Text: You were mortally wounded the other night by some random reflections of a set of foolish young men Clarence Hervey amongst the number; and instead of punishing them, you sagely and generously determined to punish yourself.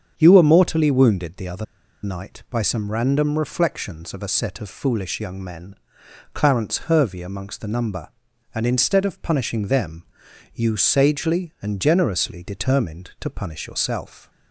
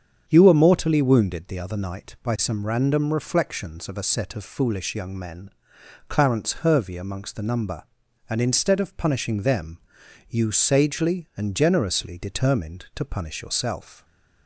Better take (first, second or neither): second